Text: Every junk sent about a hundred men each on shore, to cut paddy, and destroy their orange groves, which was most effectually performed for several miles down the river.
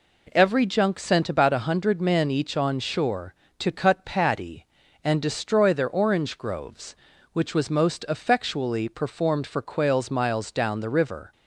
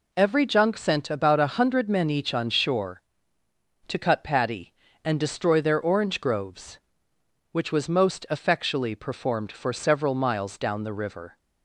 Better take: second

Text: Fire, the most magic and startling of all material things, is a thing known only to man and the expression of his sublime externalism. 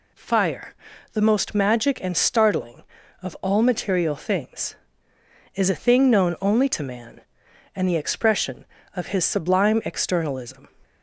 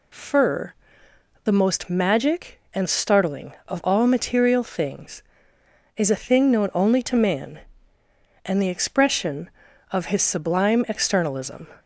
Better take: first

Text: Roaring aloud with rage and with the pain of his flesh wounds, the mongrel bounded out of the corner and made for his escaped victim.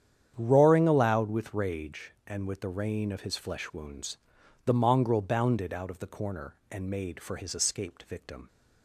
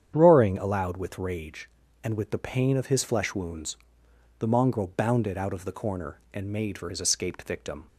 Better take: second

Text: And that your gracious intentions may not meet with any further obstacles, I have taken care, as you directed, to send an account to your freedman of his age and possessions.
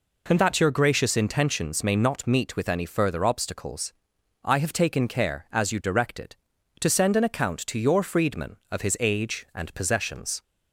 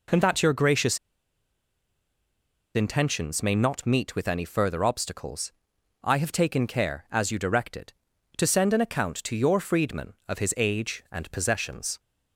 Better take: first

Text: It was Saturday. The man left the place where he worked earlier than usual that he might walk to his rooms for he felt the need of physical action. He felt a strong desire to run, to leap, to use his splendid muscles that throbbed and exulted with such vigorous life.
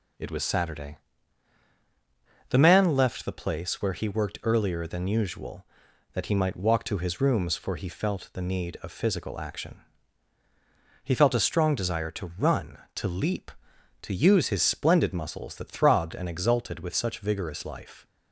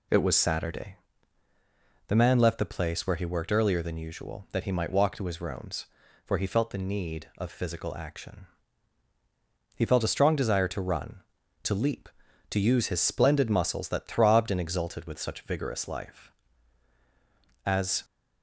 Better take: first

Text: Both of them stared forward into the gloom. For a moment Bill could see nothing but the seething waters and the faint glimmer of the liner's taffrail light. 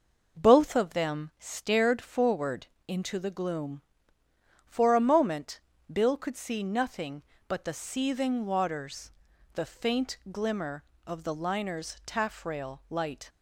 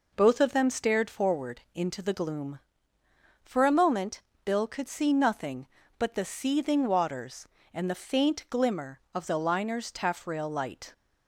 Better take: second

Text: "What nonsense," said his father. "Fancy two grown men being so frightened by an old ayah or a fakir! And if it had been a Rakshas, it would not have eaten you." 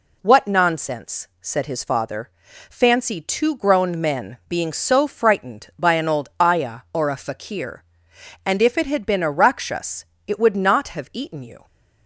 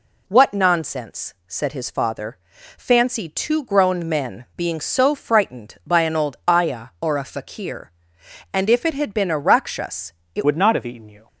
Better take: first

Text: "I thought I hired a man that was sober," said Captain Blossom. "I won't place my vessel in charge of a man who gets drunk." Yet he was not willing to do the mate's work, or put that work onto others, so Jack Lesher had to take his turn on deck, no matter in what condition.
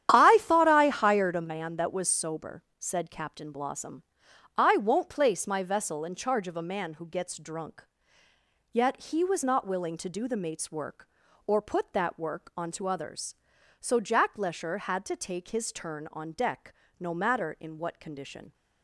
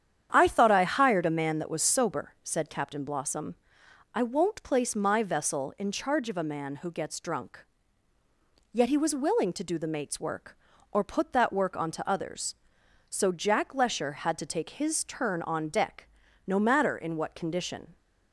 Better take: first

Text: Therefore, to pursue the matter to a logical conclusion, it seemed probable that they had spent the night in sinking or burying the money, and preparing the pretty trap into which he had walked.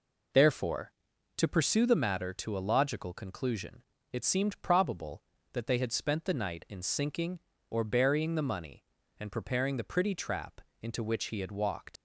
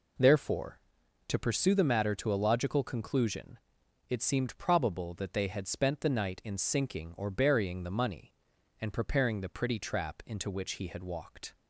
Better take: second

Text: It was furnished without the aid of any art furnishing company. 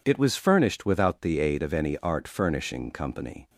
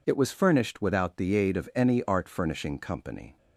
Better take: neither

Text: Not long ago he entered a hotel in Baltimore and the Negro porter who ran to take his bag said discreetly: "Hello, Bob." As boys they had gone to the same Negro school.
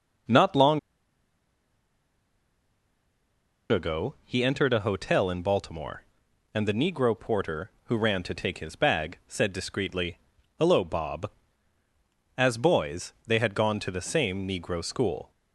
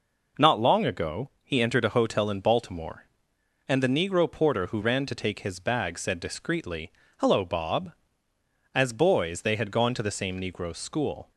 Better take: second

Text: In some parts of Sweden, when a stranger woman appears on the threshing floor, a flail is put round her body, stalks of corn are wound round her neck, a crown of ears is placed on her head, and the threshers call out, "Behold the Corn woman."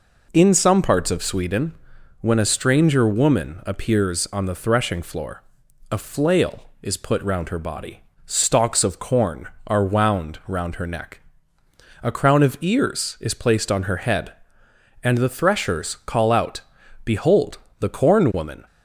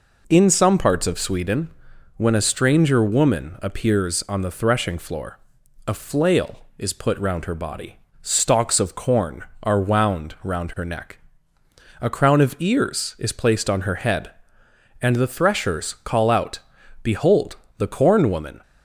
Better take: neither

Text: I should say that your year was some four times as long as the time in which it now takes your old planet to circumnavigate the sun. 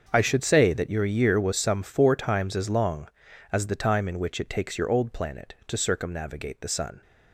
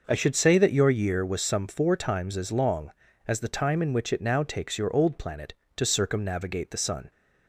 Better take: second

